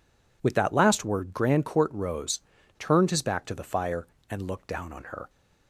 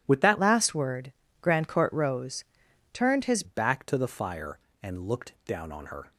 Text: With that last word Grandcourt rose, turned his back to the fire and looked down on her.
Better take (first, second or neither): first